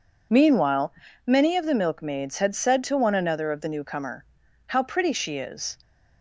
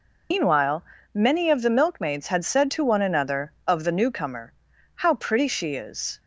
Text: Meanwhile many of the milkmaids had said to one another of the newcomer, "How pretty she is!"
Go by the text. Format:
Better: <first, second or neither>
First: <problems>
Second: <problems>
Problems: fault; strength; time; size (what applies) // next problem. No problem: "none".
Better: first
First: pauses between "Meanwhile" and "many"; slight; at 0.9 s; 0.36 s long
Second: loses the start of "Meanwhile"; at 0.3 s; 145 ms // pauses between "Meanwhile" and "many"; slight; at 0.8 s; 0.28 s long